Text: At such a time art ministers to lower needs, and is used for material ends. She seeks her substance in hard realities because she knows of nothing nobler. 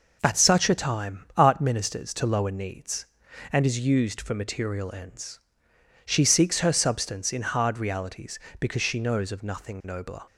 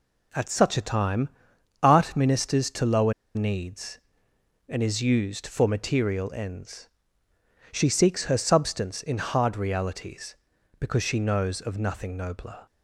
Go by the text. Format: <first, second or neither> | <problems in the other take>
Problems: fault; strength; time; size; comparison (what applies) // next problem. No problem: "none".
first | pauses between "time" and "art"; noticeable; at 1.2 s; 0.54 s long // pauses between "lower" and "needs"; slight; at 3.1 s; 0.22 s long